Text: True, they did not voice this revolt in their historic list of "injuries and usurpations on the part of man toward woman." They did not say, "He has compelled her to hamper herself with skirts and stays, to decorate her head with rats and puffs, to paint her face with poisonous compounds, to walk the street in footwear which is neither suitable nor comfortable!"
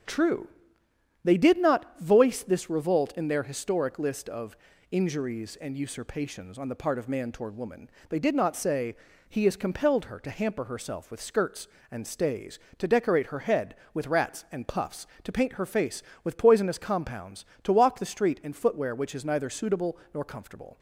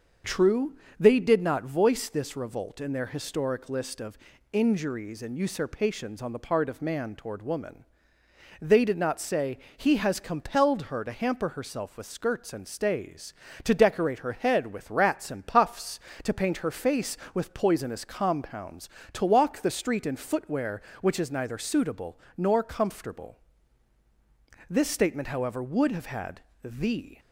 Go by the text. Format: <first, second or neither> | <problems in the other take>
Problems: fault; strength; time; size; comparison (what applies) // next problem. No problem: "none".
first | starts louder than the rest; until 1.5 s; 6.5 dB; strong in the first // pauses between "of" and "injuries"; slight; at 4.1 s; 0.34 s long; slight in the first // pauses between "suitable" and "nor"; slight; at 22.1 s; 0.20 s long; slight in the first // goes on to say "This statement however would have had the"; strong; from 24.6 s on; 2.5 s long